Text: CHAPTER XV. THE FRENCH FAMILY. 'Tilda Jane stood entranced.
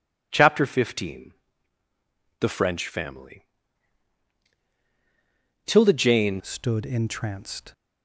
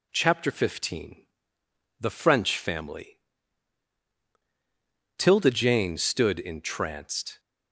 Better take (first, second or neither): second